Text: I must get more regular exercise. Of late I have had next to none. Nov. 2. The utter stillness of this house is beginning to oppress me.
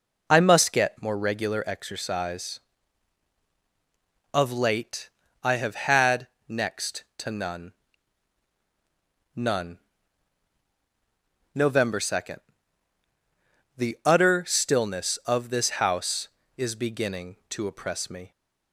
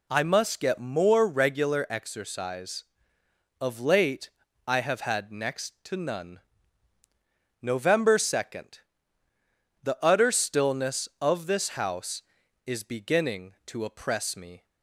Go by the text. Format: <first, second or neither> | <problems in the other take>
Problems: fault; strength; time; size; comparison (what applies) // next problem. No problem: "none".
second | pauses between "late" and "I"; slight; at 5.0 s; 0.32 s long; also in the second // pauses between "had" and "next"; slight; at 6.2 s; 0.22 s long // says "none" twice; at 9.3 s